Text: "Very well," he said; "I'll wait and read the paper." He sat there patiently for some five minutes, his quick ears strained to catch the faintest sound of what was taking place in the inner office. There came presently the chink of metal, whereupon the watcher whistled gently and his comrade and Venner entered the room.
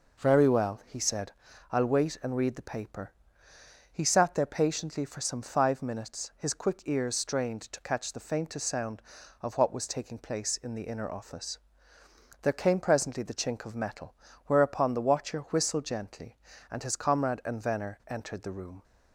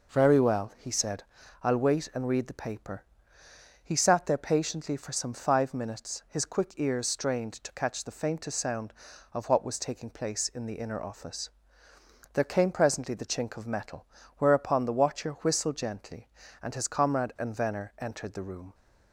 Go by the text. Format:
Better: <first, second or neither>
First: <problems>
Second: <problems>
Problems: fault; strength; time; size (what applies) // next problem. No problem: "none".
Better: neither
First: none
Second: none